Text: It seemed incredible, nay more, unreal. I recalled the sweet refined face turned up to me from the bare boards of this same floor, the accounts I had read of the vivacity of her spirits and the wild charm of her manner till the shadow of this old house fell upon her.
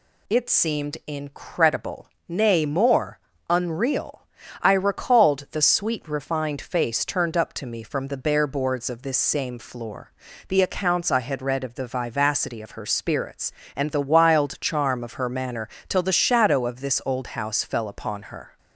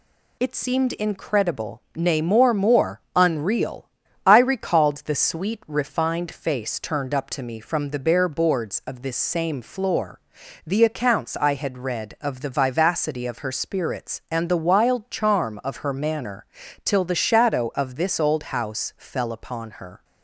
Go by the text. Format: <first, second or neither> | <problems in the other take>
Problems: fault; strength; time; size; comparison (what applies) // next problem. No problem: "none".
first | says "more" twice; at 2.5 s // pauses between "manner" and "till"; at 16.4 s; 0.38 s long; slight in the first